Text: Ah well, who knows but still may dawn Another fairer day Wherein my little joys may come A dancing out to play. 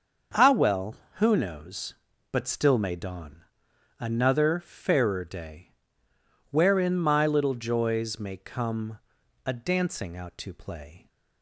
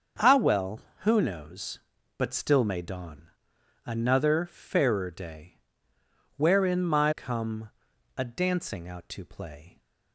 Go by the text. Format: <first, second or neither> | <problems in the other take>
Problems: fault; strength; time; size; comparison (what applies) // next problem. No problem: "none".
first | starts louder than the rest; until 1.4 s; 6.5 dB; also in the first // pauses between "dawn" and "Another"; noticeable; at 3.2 s; 0.58 s long; noticeable in the first // pauses between "day" and "Wherein"; noticeable; at 5.5 s; 0.80 s long; noticeable in the first // skips "little joys may"; at 7.1 s // pauses between "come" and "A"; noticeable; at 7.7 s; 0.46 s long; noticeable in the first